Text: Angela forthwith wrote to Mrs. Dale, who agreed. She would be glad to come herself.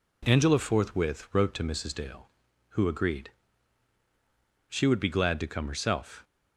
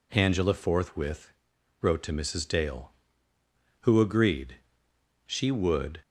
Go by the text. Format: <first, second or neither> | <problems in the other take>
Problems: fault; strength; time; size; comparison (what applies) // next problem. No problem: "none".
first | pauses between "forthwith" and "wrote"; noticeable; at 1.3 s; 0.50 s long // stops before "be glad to come herself"; at 6.0 s